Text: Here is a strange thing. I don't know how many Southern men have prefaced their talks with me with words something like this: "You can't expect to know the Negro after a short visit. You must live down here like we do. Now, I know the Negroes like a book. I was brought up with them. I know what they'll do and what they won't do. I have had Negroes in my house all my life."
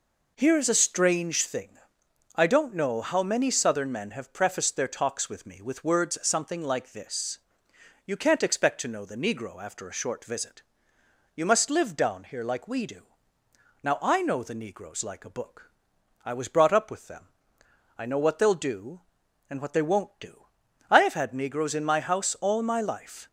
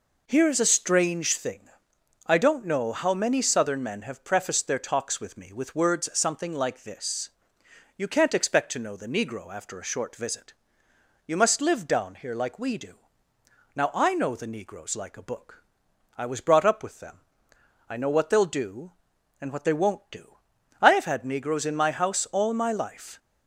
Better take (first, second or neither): neither